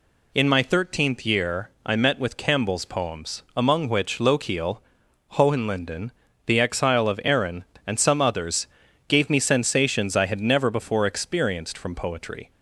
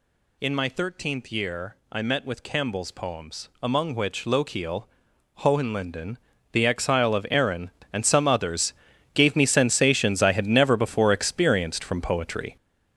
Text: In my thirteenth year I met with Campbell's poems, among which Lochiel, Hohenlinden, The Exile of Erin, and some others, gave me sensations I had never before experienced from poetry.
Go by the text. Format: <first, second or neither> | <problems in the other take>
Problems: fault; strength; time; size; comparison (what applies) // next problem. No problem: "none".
first | gets louder; strong; throughout; 8.5 dB // pauses between "year" and "I"; slight; at 1.7 s; 0.16 s long; slight in the first